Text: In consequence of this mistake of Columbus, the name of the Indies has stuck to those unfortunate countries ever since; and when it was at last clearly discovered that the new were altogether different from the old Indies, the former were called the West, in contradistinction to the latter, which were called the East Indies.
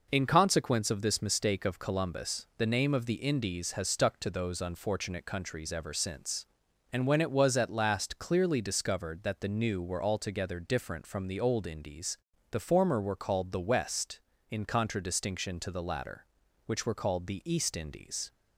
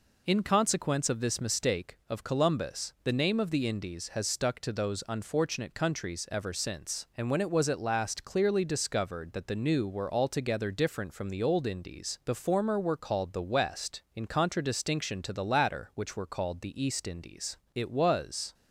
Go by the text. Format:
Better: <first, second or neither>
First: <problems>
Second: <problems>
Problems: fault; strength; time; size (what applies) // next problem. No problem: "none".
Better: first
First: none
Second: goes on to say "It was"; noticeable; from 17.7 s on; 0.80 s long